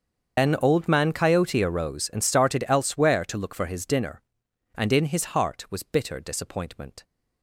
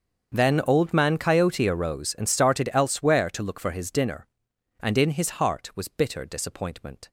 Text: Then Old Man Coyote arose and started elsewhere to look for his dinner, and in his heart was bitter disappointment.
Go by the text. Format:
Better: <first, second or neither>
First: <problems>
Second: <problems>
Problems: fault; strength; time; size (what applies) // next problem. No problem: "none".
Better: second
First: loses the start of "Then"; at 0.3 s; 105 ms // starts louder than the rest; until 1.4 s; 7 dB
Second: starts louder than the rest; until 1.3 s; 7 dB